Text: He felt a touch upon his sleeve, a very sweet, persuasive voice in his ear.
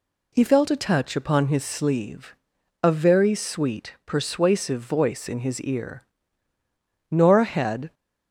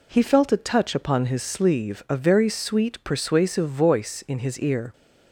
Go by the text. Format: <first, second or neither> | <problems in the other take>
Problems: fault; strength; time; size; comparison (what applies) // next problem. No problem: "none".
second | goes on to say "Nora had"; noticeable; from 7.1 s on; 0.82 s long